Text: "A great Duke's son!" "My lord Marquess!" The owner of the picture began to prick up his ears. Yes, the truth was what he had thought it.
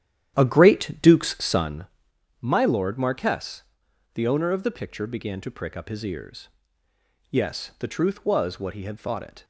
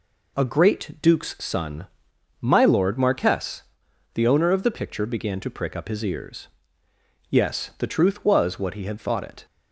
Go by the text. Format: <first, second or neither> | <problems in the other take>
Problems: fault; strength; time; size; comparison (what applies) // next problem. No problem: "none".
second | starts louder than the rest; strong; until 1.8 s; 10.5 dB